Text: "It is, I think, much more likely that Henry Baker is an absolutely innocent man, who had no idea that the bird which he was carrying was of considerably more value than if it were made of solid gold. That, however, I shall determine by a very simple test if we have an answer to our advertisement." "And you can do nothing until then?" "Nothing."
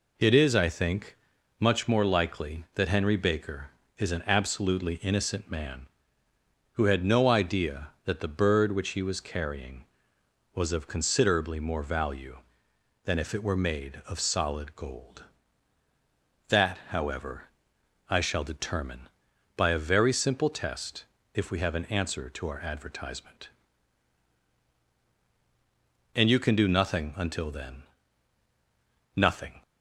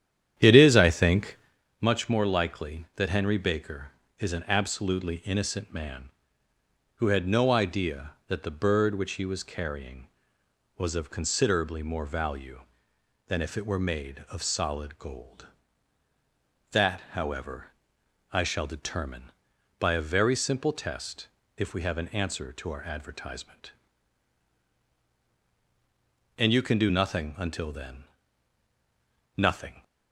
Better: first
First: pauses between "test" and "if"; slight; at 21.0 s; 0.28 s long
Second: starts louder than the rest; strong; until 1.6 s; 10 dB // pauses between "test" and "if"; slight; at 21.2 s; 0.28 s long

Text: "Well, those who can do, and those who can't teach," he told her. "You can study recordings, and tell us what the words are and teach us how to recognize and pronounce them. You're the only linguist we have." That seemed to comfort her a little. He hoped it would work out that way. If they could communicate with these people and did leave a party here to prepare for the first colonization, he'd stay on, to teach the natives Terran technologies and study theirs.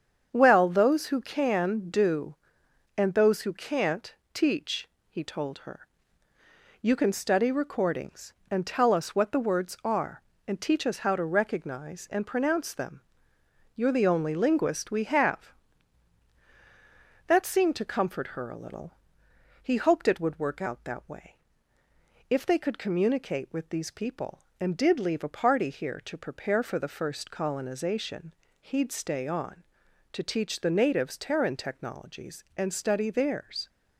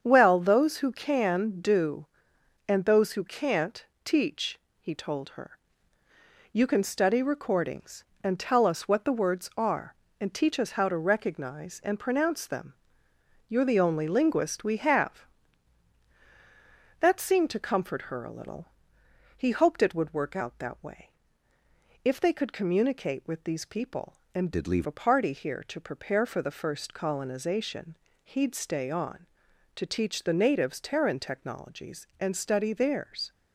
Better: first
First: starts louder than the rest; strong; until 1.3 s; 7.5 dB // pauses between "can't" and "teach"; slight; at 4.1 s; 0.18 s long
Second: starts louder than the rest; strong; until 1.0 s; 7.5 dB // pauses between "can't" and "teach"; slight; at 3.8 s; 0.18 s long // changes voice from "did" to "leave"; from 24.5 to 24.8 s; 0.3 s long

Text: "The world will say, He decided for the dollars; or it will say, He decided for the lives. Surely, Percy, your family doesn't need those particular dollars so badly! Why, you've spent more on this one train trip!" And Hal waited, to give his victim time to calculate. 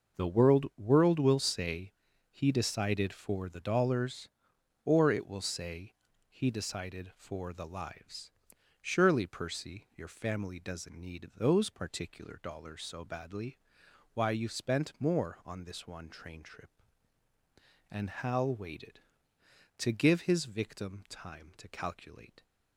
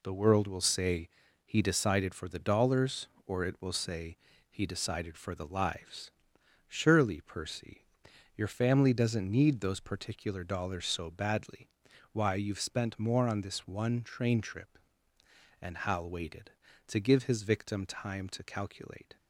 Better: second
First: says "world" twice; at 0.7 s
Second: none

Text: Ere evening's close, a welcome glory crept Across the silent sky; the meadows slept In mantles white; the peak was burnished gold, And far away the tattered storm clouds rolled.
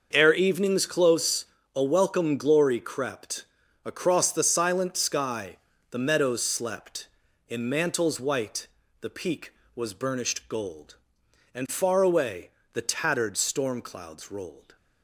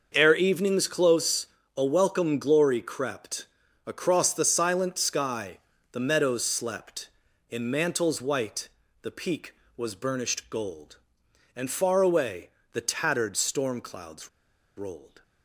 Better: first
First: starts louder than the rest; until 1.1 s; 6.5 dB // pauses between "crept" and "Across"; at 3.4 s; 0.40 s long // pauses between "away" and "the"; slight; at 12.5 s; 0.22 s long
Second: starts louder than the rest; until 1.1 s; 6.5 dB // pauses between "crept" and "Across"; at 3.4 s; 0.40 s long // pauses between "away" and "the"; slight; at 12.5 s; 0.22 s long // pauses between "clouds" and "rolled"; noticeable; at 14.2 s; 0.47 s long

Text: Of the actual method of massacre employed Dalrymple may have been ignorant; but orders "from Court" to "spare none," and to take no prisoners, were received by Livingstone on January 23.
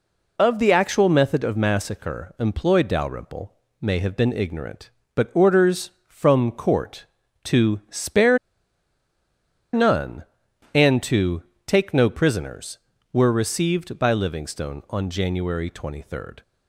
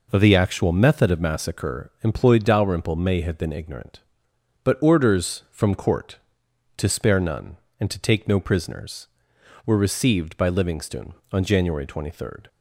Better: second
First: pauses between "Dalrymple" and "may"; slight; at 3.5 s; 0.26 s long // pauses between "spare" and "none"; strong; at 8.3 s; 1.3 s long // pauses between "to" and "take"; slight; at 11.4 s; 0.22 s long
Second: none

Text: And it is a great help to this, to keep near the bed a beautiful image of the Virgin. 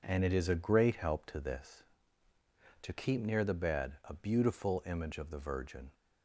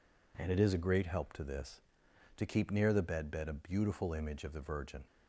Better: first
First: none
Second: says "bed" twice; at 3.2 s

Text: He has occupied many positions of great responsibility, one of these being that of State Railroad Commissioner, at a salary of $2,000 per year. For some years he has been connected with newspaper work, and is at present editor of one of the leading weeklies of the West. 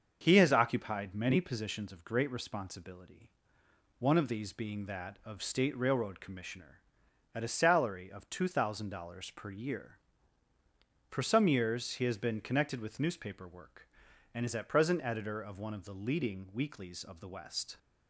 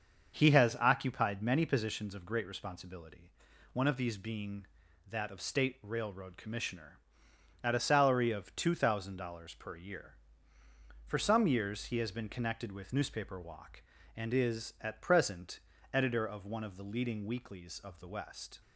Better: first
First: starts louder than the rest; until 1.2 s; 6.5 dB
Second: starts louder than the rest; until 1.4 s; 6.5 dB // says "walk" for "work"; at 13.3 s // pauses between "present" and "editor"; slight; at 15.5 s; 0.34 s long

